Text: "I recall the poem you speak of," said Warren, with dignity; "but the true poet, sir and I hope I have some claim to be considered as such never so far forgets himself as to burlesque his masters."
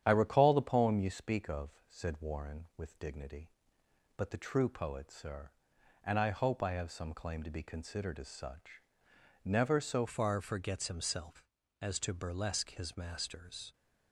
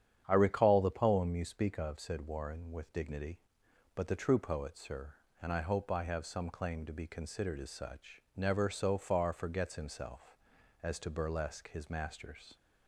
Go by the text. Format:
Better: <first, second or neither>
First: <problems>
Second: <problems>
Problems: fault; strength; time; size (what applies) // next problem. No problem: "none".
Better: second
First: starts louder than the rest; strong; until 1.0 s; 9.5 dB // pauses between "such" and "never"; noticeable; at 8.8 s; 0.62 s long // changes voice at "far"; from 10.0 s on; 3.7 s long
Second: starts louder than the rest; strong; until 1.2 s; 9 dB